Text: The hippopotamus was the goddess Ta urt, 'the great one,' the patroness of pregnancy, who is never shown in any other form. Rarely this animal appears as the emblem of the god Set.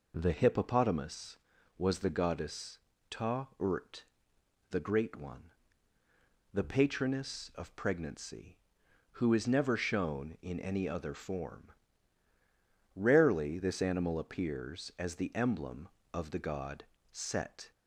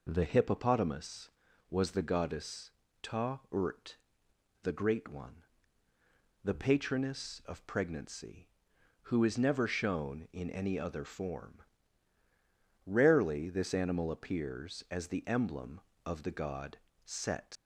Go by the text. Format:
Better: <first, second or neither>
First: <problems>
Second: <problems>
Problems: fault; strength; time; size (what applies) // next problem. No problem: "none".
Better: first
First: pauses between "goddess" and "Ta"; slight; at 2.7 s; 0.32 s long // pauses between "god" and "Set"; slight; at 16.8 s; 0.26 s long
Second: pauses between "goddess" and "Ta"; slight; at 2.6 s; 0.32 s long // pauses between "god" and "Set"; slight; at 16.7 s; 0.26 s long // leaves "Set" unfinished; at 17.5 s; 85 ms